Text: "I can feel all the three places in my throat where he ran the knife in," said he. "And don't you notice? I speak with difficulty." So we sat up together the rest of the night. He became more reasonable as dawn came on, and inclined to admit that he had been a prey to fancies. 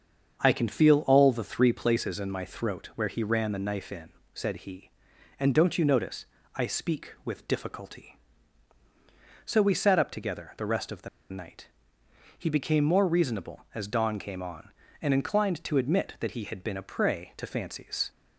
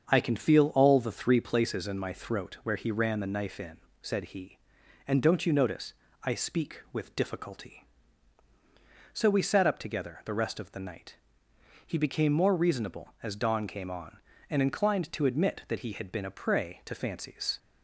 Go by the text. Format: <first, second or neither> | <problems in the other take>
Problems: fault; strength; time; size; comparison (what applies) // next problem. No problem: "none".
second | starts louder than the rest; until 1.4 s; 7 dB; also in the second // pauses between "the" and "night"; slight; at 11.0 s; 0.23 s long